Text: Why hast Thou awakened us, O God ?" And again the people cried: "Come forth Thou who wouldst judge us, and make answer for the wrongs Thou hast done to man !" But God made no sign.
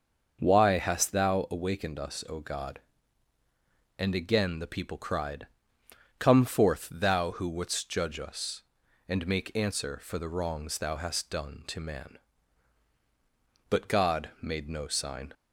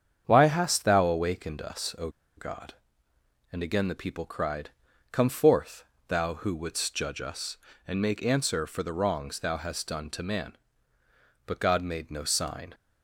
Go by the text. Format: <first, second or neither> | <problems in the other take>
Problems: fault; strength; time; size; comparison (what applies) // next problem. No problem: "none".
first | starts louder than the rest; strong; until 1.2 s; 8 dB; noticeable in the first // pauses between "O" and "God"; slight; at 2.0 s; 0.28 s long // pauses between "forth" and "Thou"; slight; at 5.8 s; 0.24 s long